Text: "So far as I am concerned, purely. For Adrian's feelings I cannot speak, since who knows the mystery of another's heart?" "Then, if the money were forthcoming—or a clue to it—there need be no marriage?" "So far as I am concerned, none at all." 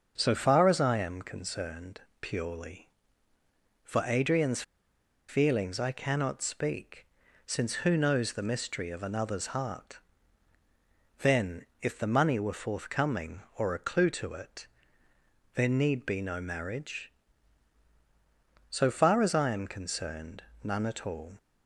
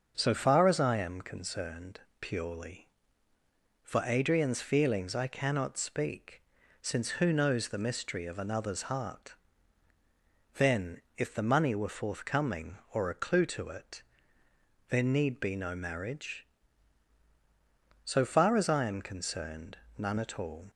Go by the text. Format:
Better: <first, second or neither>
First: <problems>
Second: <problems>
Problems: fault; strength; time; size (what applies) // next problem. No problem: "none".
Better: second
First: starts louder than the rest; until 1.1 s; 7 dB // pauses between "Adrian's" and "feelings"; noticeable; at 4.6 s; 0.66 s long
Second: starts louder than the rest; until 1.1 s; 7 dB